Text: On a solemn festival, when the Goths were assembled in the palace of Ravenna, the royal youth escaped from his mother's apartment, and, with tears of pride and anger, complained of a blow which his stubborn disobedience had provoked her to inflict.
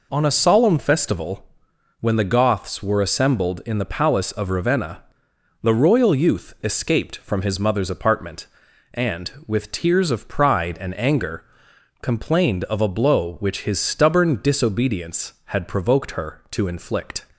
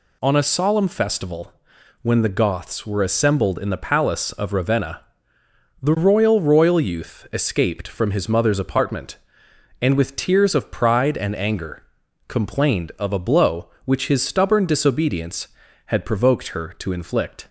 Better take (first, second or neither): first